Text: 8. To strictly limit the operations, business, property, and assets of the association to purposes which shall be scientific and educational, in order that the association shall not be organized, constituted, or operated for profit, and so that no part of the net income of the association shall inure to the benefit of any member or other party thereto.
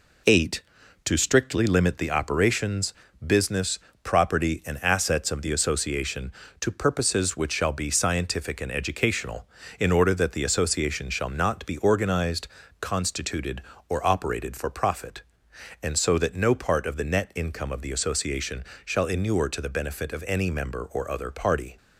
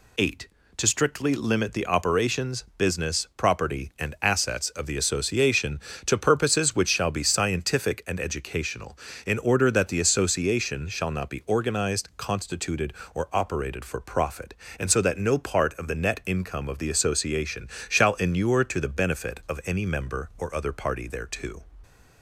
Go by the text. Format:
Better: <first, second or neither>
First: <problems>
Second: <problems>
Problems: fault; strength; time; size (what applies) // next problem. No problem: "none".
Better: second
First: pauses between "association" and "shall"; slight; at 18.6 s; 0.20 s long // stops before "thereto"; at 21.7 s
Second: pauses between "association" and "shall"; slight; at 17.6 s; 0.22 s long